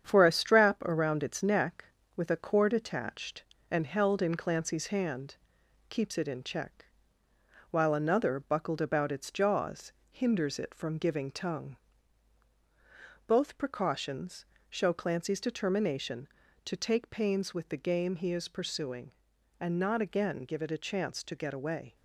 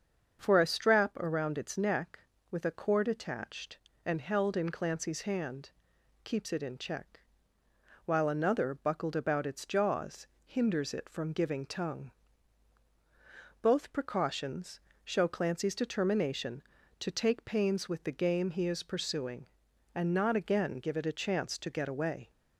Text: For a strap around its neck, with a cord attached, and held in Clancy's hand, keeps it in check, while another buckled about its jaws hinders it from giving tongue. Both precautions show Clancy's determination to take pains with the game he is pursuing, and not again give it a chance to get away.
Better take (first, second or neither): second